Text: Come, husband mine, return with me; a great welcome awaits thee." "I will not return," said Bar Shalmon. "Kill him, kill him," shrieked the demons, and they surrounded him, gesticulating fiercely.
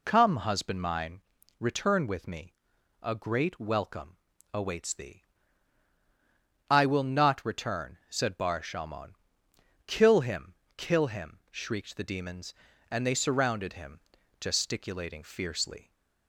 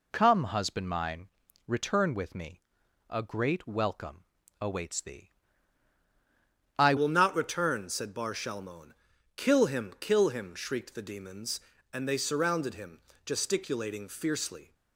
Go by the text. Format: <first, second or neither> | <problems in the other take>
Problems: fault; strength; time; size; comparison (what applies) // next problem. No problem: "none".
first | pauses between "welcome" and "awaits"; slight; at 4.2 s; 0.36 s long; slight in the first // changes voice at "will"; from 6.9 s on; 7.8 s long